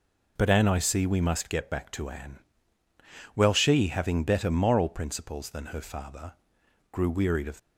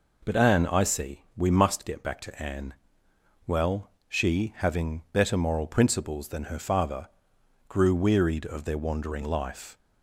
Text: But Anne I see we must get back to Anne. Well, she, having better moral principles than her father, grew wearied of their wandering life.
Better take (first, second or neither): second